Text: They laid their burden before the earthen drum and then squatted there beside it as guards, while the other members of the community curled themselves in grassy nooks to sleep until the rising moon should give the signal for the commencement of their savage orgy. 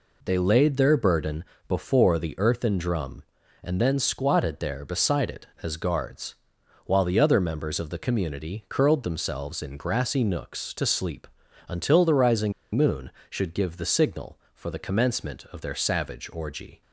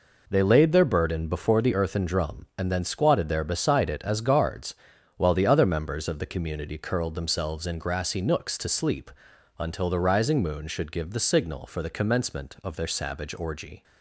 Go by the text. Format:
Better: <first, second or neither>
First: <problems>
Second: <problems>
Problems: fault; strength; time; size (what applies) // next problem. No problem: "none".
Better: second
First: pauses between "burden" and "before"; slight; at 1.4 s; 0.24 s long // pauses between "sleep" and "until"; at 11.2 s; 0.40 s long // pauses between "rising" and "moon"; slight; at 12.5 s; 0.22 s long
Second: pauses between "sleep" and "until"; noticeable; at 9.1 s; 0.48 s long